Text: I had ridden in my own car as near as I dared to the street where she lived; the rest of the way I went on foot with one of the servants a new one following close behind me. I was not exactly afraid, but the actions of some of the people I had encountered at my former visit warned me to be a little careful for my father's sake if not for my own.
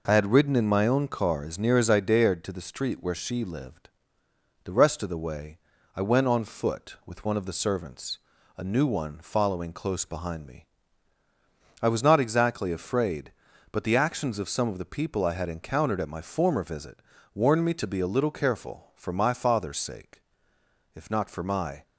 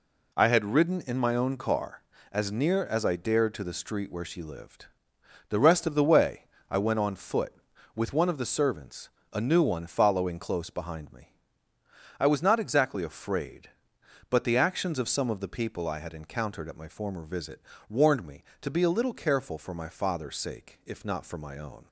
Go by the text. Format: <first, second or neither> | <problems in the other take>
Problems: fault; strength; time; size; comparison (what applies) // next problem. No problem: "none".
second | pauses between "way" and "I"; at 5.5 s; 0.38 s long; slight in the second // pauses between "servants" and "a"; slight; at 8.2 s; 0.36 s long; slight in the second // pauses between "visit" and "warned"; slight; at 17.0 s; 0.32 s long; slight in the second // pauses between "sake" and "if"; noticeable; at 20.2 s; 0.73 s long // stops before "own"; at 21.8 s